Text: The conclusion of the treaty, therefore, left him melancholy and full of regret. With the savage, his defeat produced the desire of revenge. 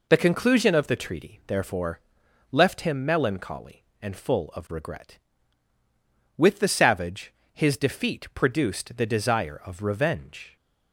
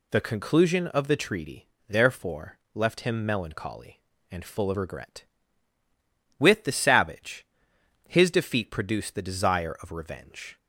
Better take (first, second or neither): neither